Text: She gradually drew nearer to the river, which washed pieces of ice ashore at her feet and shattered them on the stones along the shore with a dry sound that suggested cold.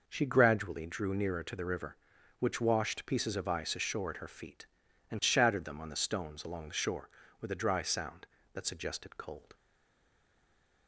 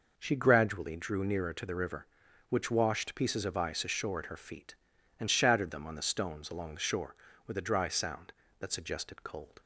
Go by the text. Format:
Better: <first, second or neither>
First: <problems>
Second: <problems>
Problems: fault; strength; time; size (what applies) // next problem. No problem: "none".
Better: second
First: stays silent after the last word; noticeable; from 9.5 s on; 1.3 s long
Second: none